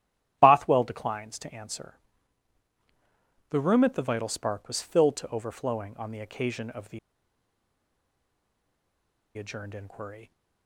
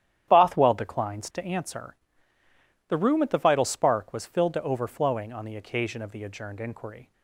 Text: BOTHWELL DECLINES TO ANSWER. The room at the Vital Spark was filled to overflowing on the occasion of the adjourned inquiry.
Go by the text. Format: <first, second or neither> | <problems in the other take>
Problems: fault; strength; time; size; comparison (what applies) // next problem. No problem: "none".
second | starts louder than the rest; strong; until 1.4 s; 11.5 dB; strong in the second // pauses between "the" and "adjourned"; strong; at 6.9 s; 2.3 s long